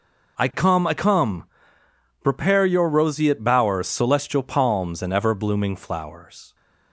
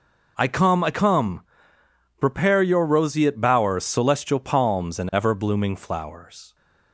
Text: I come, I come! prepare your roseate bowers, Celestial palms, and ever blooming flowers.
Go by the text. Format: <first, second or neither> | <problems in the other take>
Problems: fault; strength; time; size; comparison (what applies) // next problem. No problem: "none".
neither | none